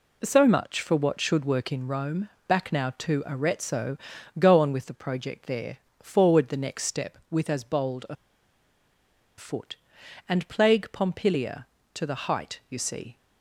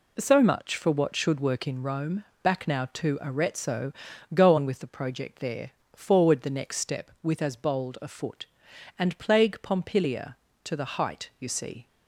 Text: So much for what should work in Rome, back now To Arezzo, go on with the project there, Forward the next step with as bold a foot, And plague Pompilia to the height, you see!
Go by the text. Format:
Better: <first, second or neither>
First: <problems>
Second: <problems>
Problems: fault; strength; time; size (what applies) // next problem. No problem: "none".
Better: second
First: pauses between "a" and "foot"; at 8.1 s; 1.2 s long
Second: none